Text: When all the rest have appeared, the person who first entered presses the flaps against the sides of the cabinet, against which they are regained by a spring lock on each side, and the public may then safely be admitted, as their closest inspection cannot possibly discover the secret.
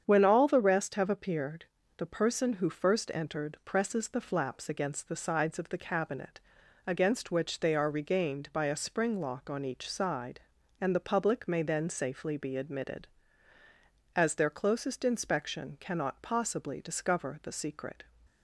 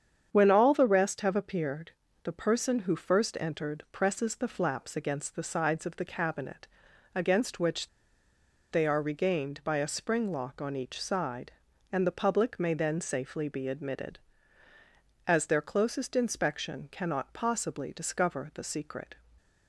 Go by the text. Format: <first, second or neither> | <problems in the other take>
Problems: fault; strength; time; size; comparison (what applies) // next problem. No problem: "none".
first | starts louder than the rest; strong; until 1.3 s; 8 dB; strong in the first // pauses between "which" and "they"; noticeable; at 7.8 s; 0.83 s long